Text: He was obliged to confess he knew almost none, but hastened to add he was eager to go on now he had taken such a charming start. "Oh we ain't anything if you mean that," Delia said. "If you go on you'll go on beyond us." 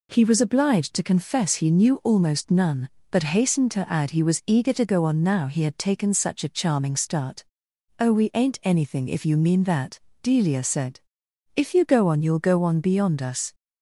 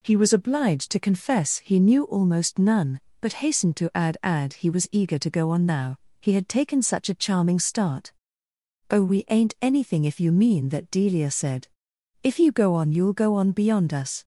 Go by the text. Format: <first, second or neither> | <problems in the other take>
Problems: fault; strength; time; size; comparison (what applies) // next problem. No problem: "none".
first | says "add" twice; at 4.2 s // pauses between "now" and "he"; slight; at 5.9 s; 0.24 s long